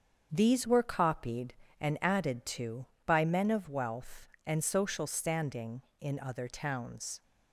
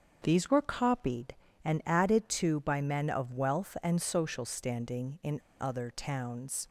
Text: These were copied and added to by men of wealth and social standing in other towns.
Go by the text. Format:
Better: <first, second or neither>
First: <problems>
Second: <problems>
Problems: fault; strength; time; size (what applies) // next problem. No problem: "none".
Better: first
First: starts louder than the rest; strong; until 1.3 s; 7 dB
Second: starts louder than the rest; until 1.2 s; 7 dB // pauses between "in" and "other"; slight; at 5.3 s; 0.21 s long